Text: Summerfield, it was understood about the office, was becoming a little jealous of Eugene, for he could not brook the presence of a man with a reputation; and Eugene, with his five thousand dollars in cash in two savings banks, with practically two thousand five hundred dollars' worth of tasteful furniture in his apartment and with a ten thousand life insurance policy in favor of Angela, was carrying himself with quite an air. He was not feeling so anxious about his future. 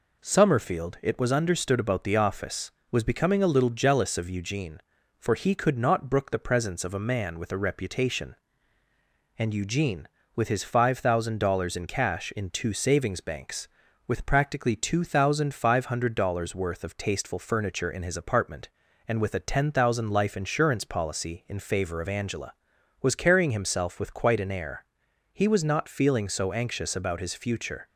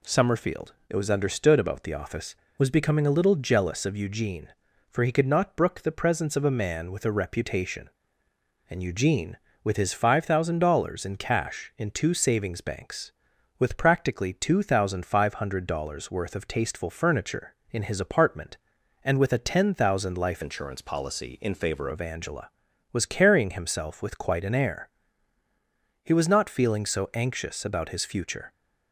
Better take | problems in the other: first | changes voice from "insurance" to "favor"; from 20.4 to 21.8 s; 1.4 s long

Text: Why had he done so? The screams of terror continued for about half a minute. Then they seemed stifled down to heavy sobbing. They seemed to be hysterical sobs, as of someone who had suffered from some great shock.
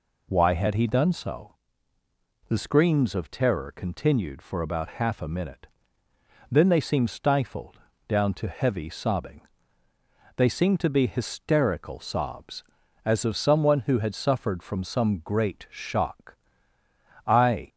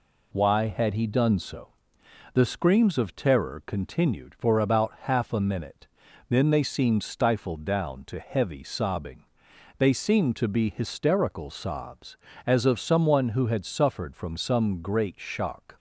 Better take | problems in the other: second | pauses between "stifled" and "down"; slight; at 7.8 s; 0.28 s long // goes on to say "I"; slight; from 17.2 s on; 0.40 s long

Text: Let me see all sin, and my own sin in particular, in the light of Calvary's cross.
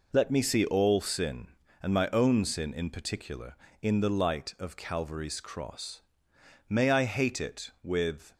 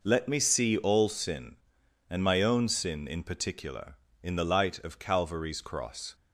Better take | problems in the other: second | goes on to say "May I hate it with"; from 6.6 s on; 1.6 s long

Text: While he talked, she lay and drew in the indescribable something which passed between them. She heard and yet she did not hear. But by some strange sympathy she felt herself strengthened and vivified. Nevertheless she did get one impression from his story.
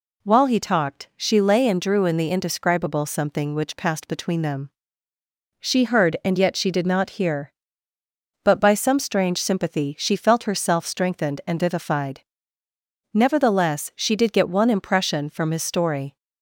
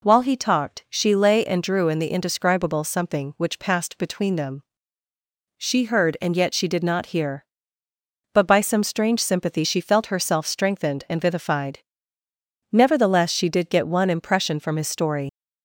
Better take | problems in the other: first | leaves "story" unfinished; at 15.2 s; 80 ms

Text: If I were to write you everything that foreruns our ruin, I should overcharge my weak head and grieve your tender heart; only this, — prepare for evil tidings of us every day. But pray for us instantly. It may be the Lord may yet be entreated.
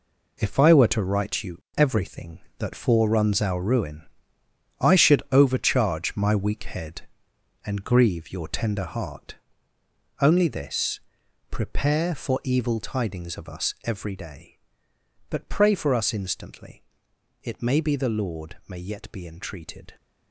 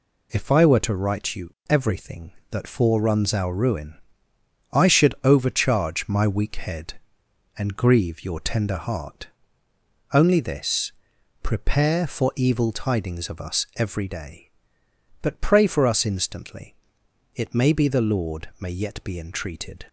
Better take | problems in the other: second | gets quieter; strong; throughout; 10 dB

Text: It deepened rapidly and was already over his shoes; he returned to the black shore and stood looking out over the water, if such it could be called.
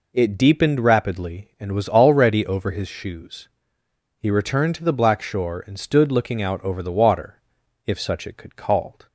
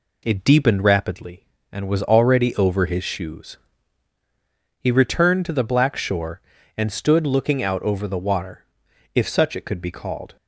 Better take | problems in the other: second | skips "be"; at 8.5 s

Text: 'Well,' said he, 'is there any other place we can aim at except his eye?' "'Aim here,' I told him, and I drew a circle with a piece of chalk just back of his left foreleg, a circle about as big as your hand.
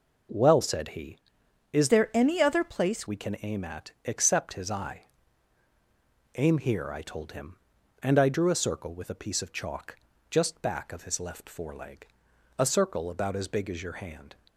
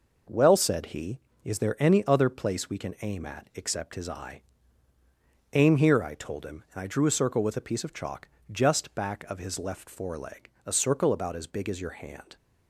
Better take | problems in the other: second | changes voice from "there" to "place"; from 1.8 to 3.0 s; 1.2 s long // pauses between "chalk" and "just"; slight; at 9.9 s; 0.34 s long; slight in the second

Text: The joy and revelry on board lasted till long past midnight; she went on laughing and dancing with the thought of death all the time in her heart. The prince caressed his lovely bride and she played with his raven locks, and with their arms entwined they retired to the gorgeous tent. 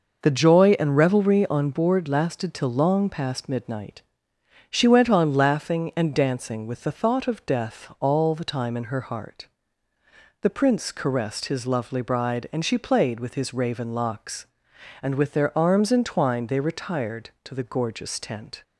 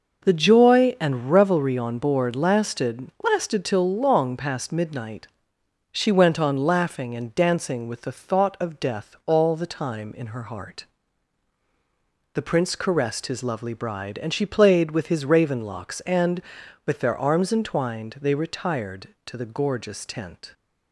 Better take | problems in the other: first | says "lasted" twice; at 3.2 s

